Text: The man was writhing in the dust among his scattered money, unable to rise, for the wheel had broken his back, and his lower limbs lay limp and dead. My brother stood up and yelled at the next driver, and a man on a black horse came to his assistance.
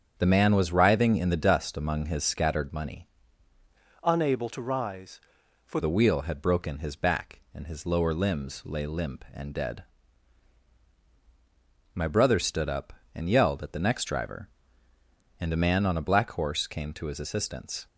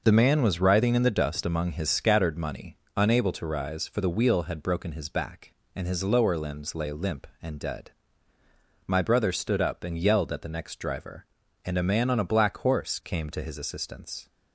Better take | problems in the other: second | starts louder than the rest; strong; until 1.1 s; 7.5 dB // changes voice from "unable" to "for"; from 4.0 to 5.7 s; 1.7 s long

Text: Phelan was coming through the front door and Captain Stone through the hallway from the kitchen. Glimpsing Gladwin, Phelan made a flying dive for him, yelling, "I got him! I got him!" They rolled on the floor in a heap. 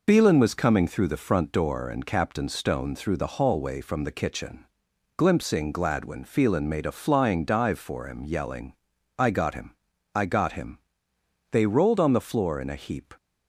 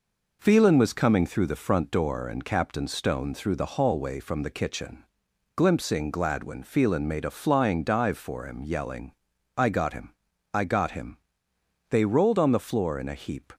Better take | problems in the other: second | loses the start of "Phelan"; at 0.0 s; 65 ms

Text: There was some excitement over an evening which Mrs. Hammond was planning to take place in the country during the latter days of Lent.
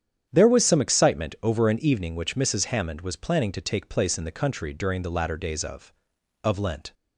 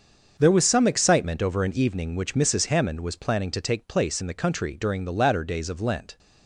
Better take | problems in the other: second | starts louder than the rest; strong; until 1.3 s; 9 dB; also in the second // says "of" twice; at 6.4 s

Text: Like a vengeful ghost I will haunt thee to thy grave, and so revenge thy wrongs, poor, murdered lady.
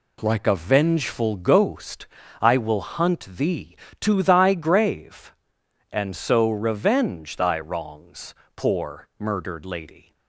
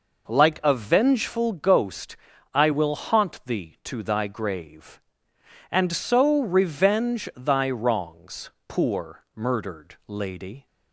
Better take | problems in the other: second | pauses between "ghost" and "I"; slight; at 2.0 s; 0.36 s long; slight in the second // says "hunt" for "haunt"; at 2.8 s

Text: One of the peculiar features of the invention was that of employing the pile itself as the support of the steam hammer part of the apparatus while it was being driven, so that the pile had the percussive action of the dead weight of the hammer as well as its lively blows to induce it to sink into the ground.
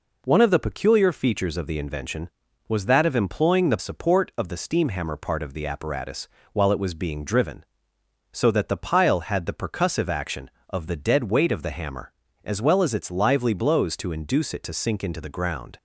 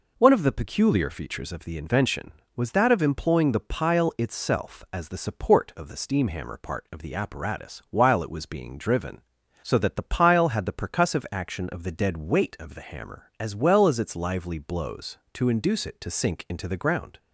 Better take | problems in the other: second | skips "pile itself as the"; at 3.7 s // pauses between "apparatus" and "while"; slight; at 6.2 s; 0.26 s long

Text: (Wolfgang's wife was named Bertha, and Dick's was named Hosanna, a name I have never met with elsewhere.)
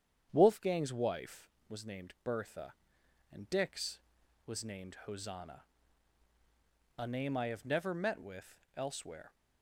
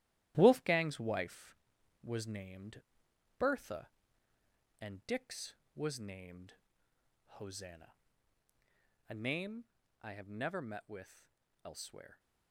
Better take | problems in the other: first | gets quieter; strong; throughout; 8 dB // starts louder than the rest; strong; until 1.3 s; 13.5 dB; strong in the first // pauses between "named" and "Bertha"; noticeable; at 2.8 s; 0.56 s long // pauses between "named" and "Hosanna"; noticeable; at 6.5 s; 0.85 s long // pauses between "name" and "I"; at 9.6 s; 0.38 s long // pauses between "with" and "elsewhere"; slight; at 11.2 s; 0.36 s long; slight in the first

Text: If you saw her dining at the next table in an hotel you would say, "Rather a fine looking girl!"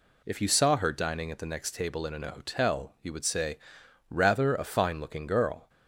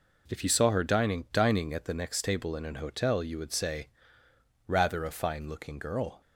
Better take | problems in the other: first | says "dining" twice; at 1.3 s

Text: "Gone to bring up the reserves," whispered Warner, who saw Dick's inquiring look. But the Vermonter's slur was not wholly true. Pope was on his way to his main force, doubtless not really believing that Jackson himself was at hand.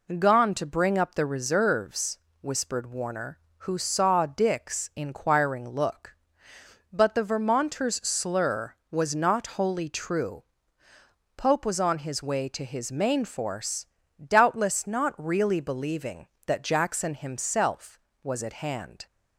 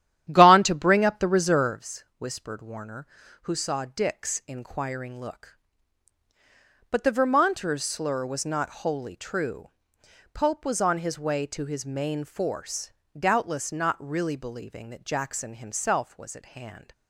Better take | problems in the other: first | starts louder than the rest; strong; until 1.9 s; 11 dB

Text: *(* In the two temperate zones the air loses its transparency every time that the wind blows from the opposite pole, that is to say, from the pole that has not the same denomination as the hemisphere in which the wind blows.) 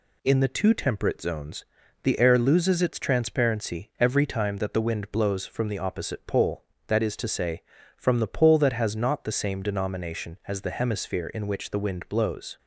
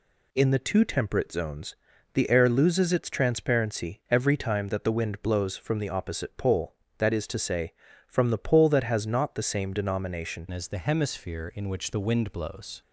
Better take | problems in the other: first | pauses between "zones" and "the"; at 1.7 s; 0.38 s long; also in the first // changes voice at "as"; from 10.5 s on; 2.3 s long

